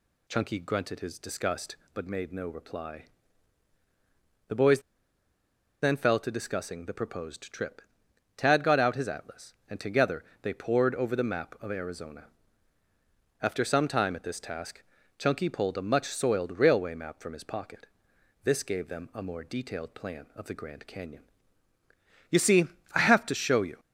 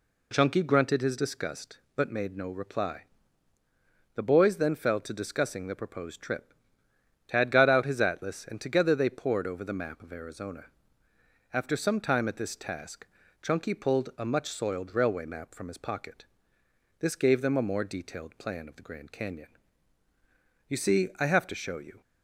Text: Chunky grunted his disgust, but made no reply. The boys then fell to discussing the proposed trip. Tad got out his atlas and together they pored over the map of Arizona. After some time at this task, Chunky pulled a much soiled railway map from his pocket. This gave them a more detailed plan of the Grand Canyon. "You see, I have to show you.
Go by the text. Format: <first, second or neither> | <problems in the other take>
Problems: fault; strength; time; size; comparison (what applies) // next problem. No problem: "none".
second | pauses between "boys" and "then"; at 4.7 s; 1.0 s long // pauses between "together" and "they"; slight; at 10.2 s; 0.20 s long